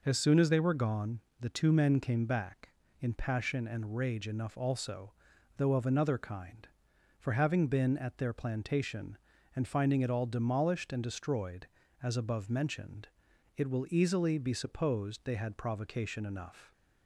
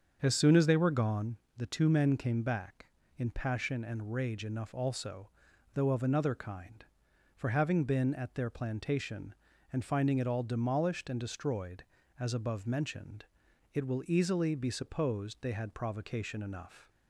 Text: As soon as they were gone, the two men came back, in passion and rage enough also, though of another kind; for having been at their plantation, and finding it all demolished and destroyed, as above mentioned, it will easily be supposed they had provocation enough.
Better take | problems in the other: first | starts louder than the rest; until 1.4 s; 7 dB

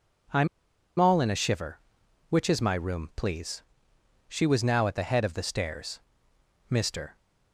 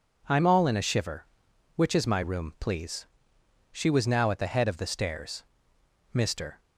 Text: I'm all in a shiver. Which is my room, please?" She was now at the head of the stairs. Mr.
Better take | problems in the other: second | pauses between "I'm" and "all"; noticeable; at 0.4 s; 0.52 s long

